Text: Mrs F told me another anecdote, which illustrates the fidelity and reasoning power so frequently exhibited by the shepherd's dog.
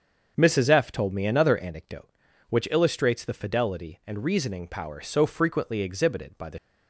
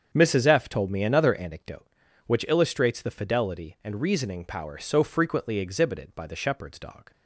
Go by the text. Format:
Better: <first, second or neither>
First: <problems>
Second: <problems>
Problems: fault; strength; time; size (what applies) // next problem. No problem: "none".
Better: second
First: starts louder than the rest; until 1.3 s; 7 dB // stops before "shepherd's dog"; at 6.5 s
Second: starts louder than the rest; strong; until 1.1 s; 7.5 dB